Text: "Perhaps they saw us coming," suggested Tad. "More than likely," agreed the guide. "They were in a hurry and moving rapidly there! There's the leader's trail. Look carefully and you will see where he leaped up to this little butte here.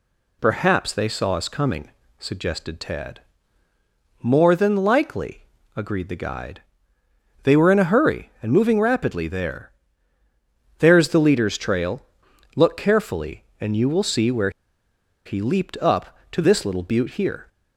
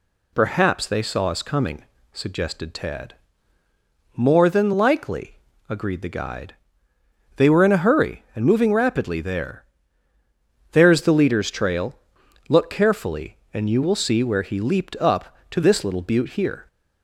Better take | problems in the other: second | pauses between "where" and "he"; noticeable; at 14.5 s; 0.74 s long

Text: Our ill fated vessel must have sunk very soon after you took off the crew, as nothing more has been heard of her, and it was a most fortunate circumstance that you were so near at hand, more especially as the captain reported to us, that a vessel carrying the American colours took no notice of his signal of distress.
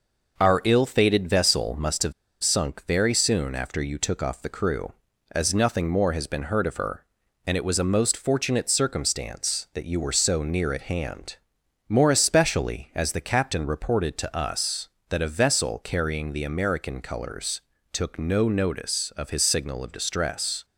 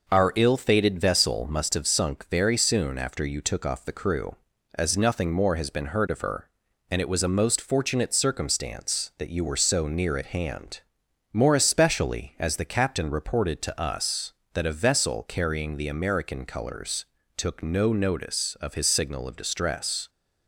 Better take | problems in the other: second | pauses between "have" and "sunk"; slight; at 2.1 s; 0.29 s long // pauses between "colours" and "took"; slight; at 17.6 s; 0.32 s long; slight in the second

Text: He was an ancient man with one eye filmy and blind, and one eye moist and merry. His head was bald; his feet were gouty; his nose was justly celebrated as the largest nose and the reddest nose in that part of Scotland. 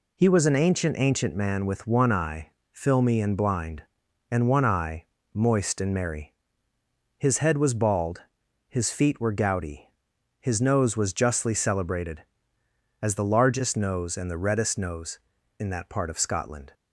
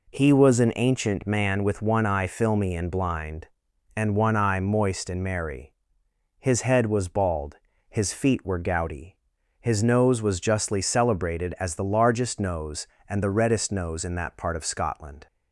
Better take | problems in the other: second | says "ancient" twice; at 0.9 s // pauses between "eye" and "filmy"; slight; at 2.5 s; 0.20 s long // pauses between "eye" and "moist"; slight; at 5.0 s; 0.28 s long

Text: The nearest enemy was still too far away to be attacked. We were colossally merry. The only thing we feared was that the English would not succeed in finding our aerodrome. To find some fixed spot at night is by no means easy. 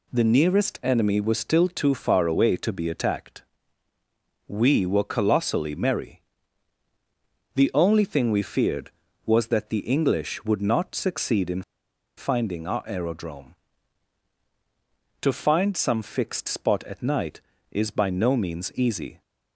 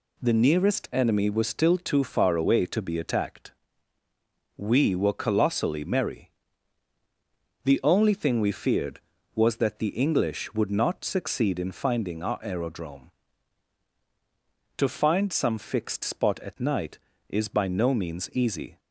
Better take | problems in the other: second | pauses between "in" and "finding"; noticeable; at 11.6 s; 0.55 s long

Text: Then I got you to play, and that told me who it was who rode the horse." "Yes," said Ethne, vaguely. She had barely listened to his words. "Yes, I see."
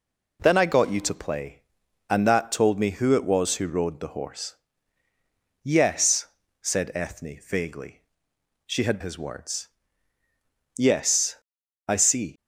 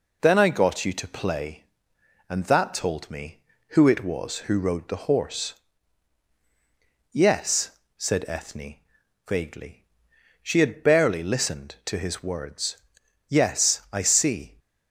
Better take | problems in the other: second | skips "barely listened to"; at 9.0 s

